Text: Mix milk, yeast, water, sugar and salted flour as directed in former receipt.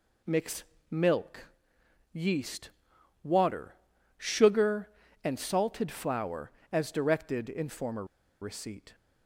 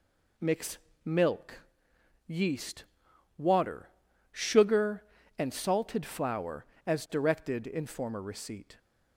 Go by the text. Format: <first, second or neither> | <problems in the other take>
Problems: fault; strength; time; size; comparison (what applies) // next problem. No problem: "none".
second | pauses between "Mix" and "milk"; slight; at 0.6 s; 0.26 s long; slight in the second // pauses between "former" and "receipt"; at 8.0 s; 0.36 s long